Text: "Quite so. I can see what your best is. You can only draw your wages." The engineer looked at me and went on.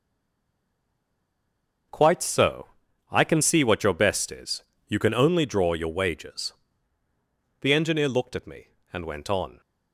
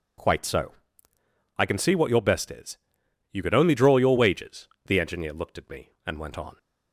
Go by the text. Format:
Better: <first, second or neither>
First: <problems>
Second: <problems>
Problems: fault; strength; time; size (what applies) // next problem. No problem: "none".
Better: second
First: stays silent before the first word; noticeable; until 1.8 s; 1.8 s long // starts louder than the rest; noticeable; until 3.3 s; 6 dB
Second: none